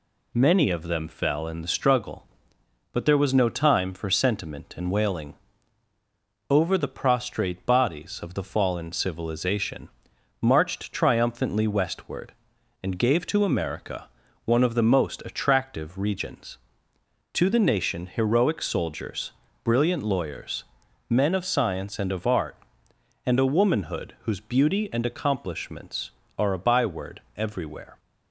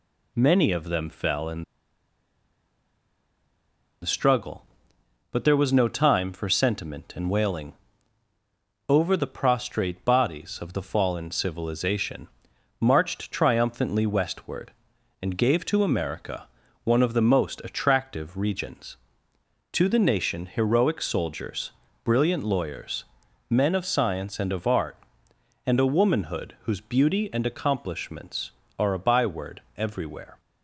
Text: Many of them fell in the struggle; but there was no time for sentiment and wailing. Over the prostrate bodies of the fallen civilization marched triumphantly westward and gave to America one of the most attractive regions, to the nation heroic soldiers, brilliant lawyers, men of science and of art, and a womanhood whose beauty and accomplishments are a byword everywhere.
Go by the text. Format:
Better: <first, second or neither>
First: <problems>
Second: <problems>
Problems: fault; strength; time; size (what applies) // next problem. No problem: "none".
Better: first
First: pauses between "civilization" and "marched"; noticeable; at 9.8 s; 0.52 s long // pauses between "America" and "one"; at 14.0 s; 0.38 s long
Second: pauses between "in" and "the"; strong; at 1.6 s; 2.4 s long // pauses between "civilization" and "marched"; noticeable; at 12.2 s; 0.52 s long // pauses between "America" and "one"; at 16.4 s; 0.38 s long